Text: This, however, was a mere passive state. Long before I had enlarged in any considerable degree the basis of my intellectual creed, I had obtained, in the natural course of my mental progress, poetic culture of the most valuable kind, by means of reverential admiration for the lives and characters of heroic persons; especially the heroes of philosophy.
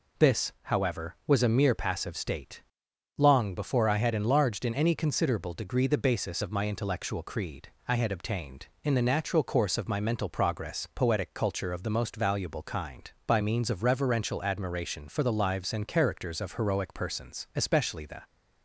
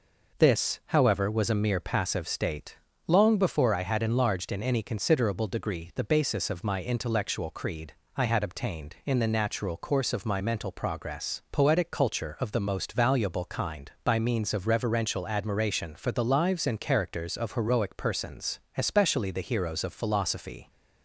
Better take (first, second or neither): second